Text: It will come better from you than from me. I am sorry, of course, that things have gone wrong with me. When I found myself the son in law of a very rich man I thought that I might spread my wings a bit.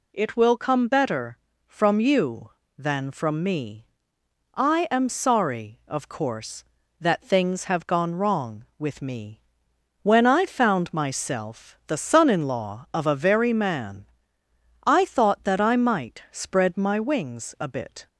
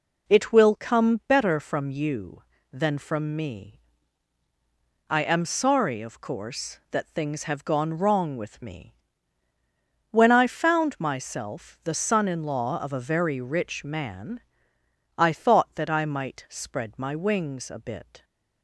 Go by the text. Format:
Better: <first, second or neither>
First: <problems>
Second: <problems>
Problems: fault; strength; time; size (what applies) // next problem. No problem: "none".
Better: second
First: skips "rich"; at 13.5 s // pauses between "man" and "I"; noticeable; at 14.0 s; 0.82 s long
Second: pauses between "man" and "I"; noticeable; at 14.4 s; 0.76 s long